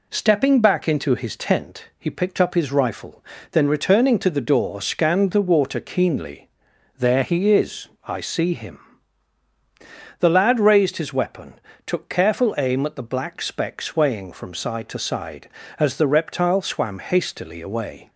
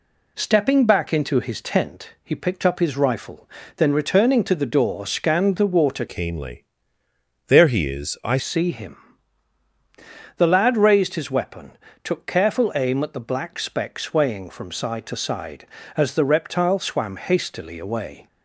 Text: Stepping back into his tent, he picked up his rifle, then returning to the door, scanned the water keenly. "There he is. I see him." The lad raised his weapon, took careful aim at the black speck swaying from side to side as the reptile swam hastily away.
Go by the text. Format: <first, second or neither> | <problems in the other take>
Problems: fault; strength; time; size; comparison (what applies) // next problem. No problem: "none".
first | changes voice from "keenly" to "I"; from 6.0 to 8.3 s; 2.3 s long